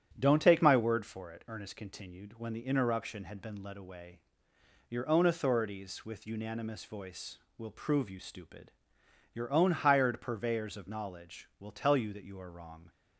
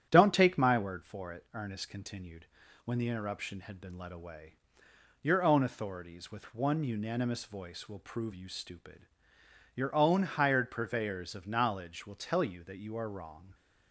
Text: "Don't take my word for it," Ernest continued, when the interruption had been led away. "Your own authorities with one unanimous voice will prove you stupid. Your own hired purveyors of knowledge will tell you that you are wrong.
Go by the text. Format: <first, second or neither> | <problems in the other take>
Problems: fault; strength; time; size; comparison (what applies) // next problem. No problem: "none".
second | starts louder than the rest; strong; until 1.1 s; 9 dB; strong in the second // skips "one"; at 6.2 s